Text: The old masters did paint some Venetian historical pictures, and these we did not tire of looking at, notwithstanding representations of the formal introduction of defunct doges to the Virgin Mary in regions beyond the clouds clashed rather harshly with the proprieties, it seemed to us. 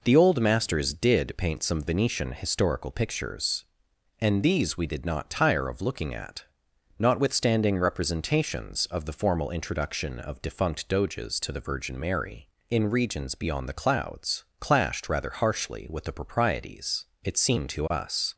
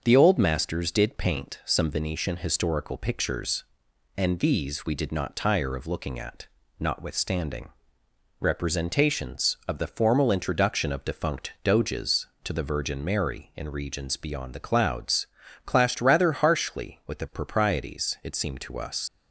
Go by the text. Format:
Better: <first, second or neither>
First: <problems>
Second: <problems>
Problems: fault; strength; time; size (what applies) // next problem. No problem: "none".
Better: first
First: pauses between "clouds" and "clashed"; slight; at 14.4 s; 0.16 s long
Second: starts louder than the rest; until 1.0 s; 6.5 dB // pauses between "notwithstanding" and "representations"; noticeable; at 7.6 s; 0.72 s long // pauses between "clouds" and "clashed"; at 15.2 s; 0.40 s long // leaves "us" unfinished; at 19.0 s; 80 ms